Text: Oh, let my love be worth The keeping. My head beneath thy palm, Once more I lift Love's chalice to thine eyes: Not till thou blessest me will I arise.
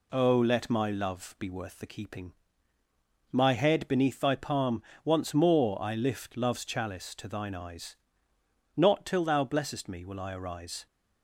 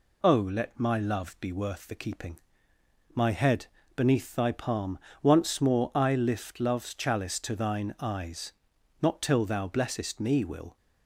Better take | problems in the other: first | pauses between "head" and "beneath"; slight; at 3.6 s; 0.30 s long // stops before "I arise"; at 10.7 s

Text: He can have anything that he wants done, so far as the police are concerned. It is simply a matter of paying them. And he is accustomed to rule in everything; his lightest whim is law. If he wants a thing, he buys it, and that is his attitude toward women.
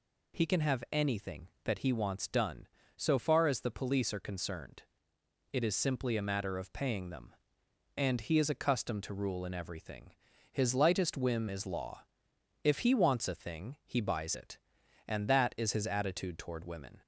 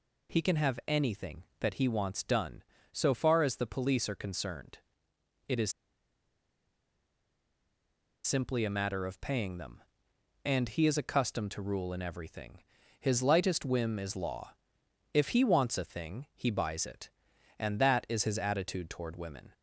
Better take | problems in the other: first | pauses between "is" and "simply"; strong; at 5.7 s; 2.5 s long

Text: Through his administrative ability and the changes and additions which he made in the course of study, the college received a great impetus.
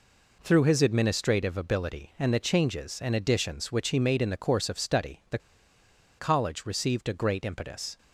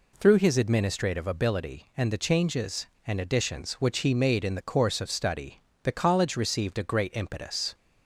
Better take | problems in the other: second | pauses between "the" and "college"; noticeable; at 5.3 s; 0.81 s long

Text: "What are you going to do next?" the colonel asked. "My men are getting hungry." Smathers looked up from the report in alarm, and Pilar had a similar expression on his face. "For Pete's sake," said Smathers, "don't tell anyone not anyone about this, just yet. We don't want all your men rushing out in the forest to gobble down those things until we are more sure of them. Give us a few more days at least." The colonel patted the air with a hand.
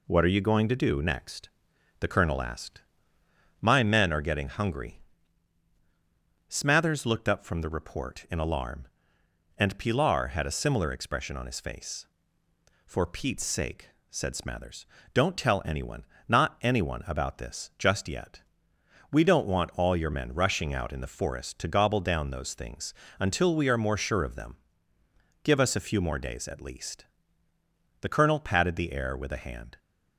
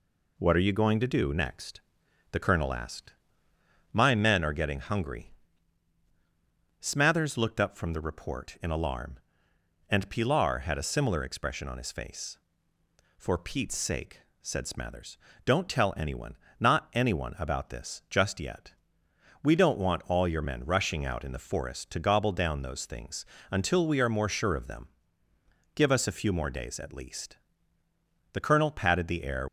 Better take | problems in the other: first | pauses between "anyone" and "not"; slight; at 16.3 s; 0.24 s long; slight in the first // pauses between "things" and "until"; slight; at 23.2 s; 0.26 s long; slight in the first // stops before "with a hand"; at 29.4 s

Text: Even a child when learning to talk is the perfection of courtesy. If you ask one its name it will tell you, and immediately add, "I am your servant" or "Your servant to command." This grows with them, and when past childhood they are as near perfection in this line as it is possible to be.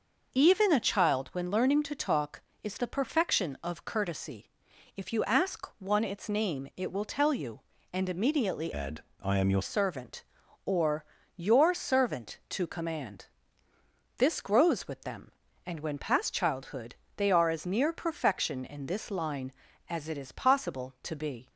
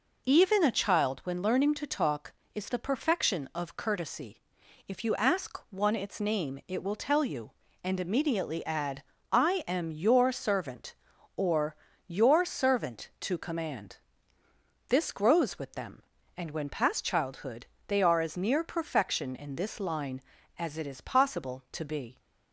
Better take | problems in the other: second | changes voice from "add" to "your"; from 8.7 to 9.6 s; 0.9 s long // pauses between "or" and "Your"; slight; at 11.0 s; 0.32 s long; slight in the second // pauses between "childhood" and "they"; slight; at 16.9 s; 0.22 s long; slight in the second

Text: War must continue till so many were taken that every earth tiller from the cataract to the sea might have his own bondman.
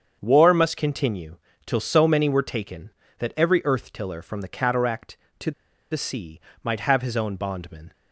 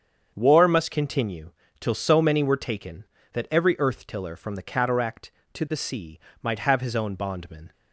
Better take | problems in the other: second | starts louder than the rest; strong; until 1.2 s; 7.5 dB; strong in the second // pauses between "continue" and "till"; slight; at 1.3 s; 0.28 s long; slight in the second // pauses between "to" and "the"; at 5.5 s; 0.40 s long // pauses between "sea" and "might"; slight; at 6.4 s; 0.22 s long; slight in the second

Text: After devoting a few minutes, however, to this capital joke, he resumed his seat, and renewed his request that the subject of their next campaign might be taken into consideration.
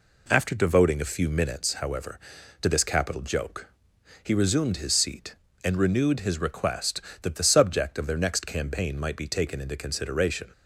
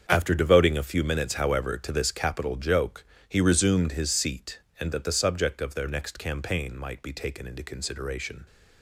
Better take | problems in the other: first | starts louder than the rest; strong; until 1.1 s; 7 dB // skips "renewed his request"; at 4.9 s

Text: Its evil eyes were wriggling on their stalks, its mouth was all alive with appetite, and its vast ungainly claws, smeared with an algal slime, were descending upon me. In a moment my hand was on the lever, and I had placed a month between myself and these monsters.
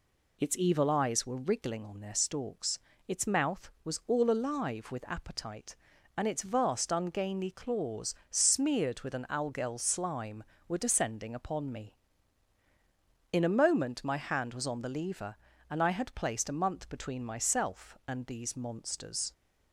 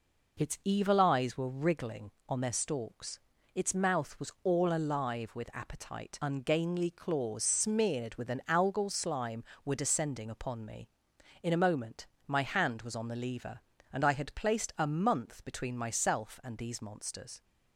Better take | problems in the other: first | skips "and its vast"; at 6.2 s // pauses between "moment" and "my"; slight; at 12.0 s; 0.18 s long

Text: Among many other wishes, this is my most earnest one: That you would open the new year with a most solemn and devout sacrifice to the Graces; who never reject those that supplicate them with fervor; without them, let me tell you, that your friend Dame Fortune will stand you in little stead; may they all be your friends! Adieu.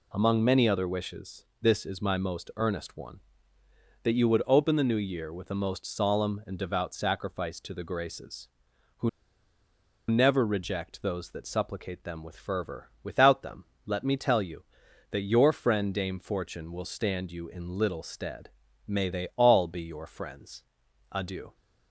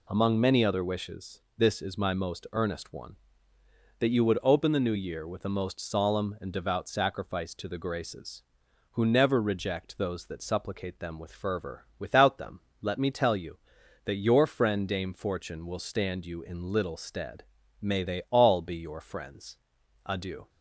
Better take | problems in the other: second | pauses between "who" and "never"; at 9.0 s; 0.99 s long

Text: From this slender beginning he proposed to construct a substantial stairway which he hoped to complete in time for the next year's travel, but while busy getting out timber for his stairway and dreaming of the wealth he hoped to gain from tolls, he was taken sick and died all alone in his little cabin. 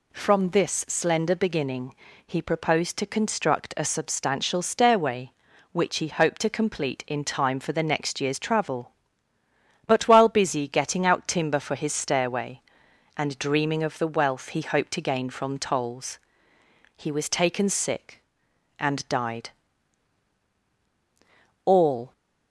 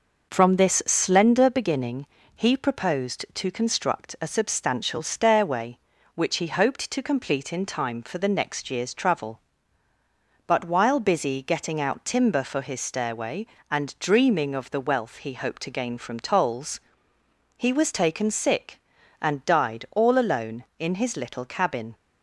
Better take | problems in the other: second | pauses between "beginning" and "he"; slight; at 1.9 s; 0.32 s long; slight in the second // pauses between "died" and "all"; strong; at 19.5 s; 2.1 s long // stops before "alone in his little cabin"; at 22.1 s

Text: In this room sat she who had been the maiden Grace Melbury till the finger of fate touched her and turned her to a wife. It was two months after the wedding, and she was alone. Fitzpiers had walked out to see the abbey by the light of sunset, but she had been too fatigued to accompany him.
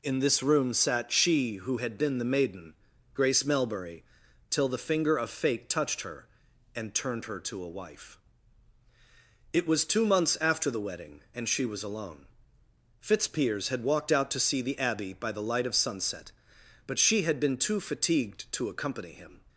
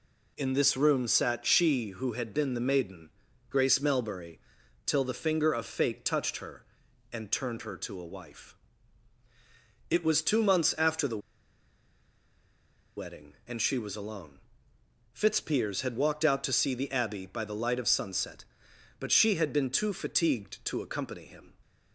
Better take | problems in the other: first | pauses between "maiden" and "Grace"; at 3.1 s; 0.40 s long; also in the first // pauses between "Melbury" and "till"; noticeable; at 4.4 s; 0.46 s long; noticeable in the first // pauses between "the" and "wedding"; strong; at 11.1 s; 1.7 s long

